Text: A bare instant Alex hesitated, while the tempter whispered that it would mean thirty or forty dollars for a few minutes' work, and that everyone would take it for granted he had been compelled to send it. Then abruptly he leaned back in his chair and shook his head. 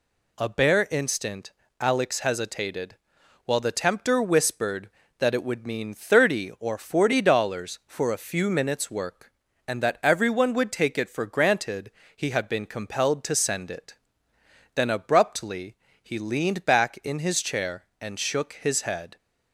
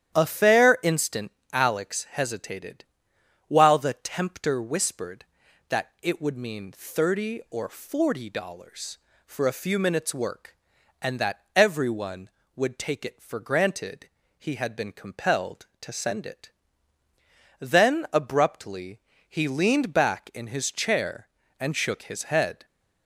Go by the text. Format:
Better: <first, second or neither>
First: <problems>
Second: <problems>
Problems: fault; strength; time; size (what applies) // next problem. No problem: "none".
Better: first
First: pauses between "instant" and "Alex"; slight; at 1.5 s; 0.28 s long // pauses between "granted" and "he"; slight; at 11.9 s; 0.24 s long // pauses between "abruptly" and "he"; slight; at 15.7 s; 0.26 s long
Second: starts louder than the rest; strong; until 1.2 s; 10.5 dB // says "fair" for "bare"; at 0.2 s // pauses between "instant" and "Alex"; slight; at 1.3 s; 0.22 s long // pauses between "granted" and "he"; slight; at 14.0 s; 0.32 s long // pauses between "abruptly" and "he"; slight; at 18.9 s; 0.28 s long